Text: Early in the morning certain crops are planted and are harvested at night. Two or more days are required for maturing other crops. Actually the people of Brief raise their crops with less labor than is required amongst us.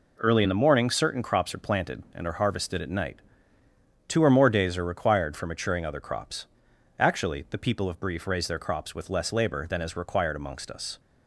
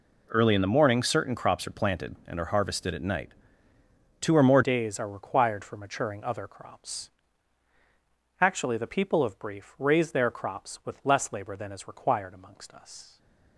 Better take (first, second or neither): first